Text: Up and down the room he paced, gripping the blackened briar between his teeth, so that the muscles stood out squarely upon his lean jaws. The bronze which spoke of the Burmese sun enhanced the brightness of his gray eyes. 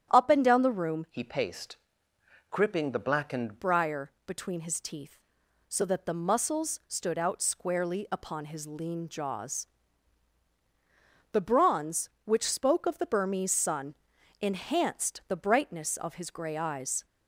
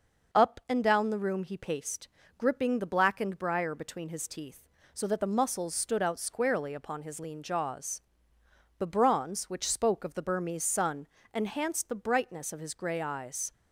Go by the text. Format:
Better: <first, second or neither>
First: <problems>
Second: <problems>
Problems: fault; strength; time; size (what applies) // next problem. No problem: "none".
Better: second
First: starts louder than the rest; strong; until 1.1 s; 9.5 dB // changes voice from "he" to "blackened"; from 1.1 to 3.6 s; 2.5 s long // pauses between "briar" and "between"; slight; at 4.1 s; 0.16 s long // pauses between "sun" and "enhanced"; noticeable; at 13.9 s; 0.46 s long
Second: pauses between "sun" and "enhanced"; slight; at 11.0 s; 0.26 s long